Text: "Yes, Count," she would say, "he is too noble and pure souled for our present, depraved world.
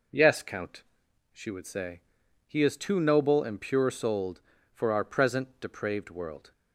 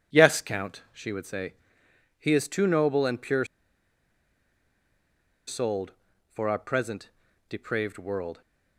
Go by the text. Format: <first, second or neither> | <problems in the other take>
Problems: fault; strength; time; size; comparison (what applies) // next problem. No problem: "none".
first | pauses between "pure" and "souled"; strong; at 3.4 s; 2.0 s long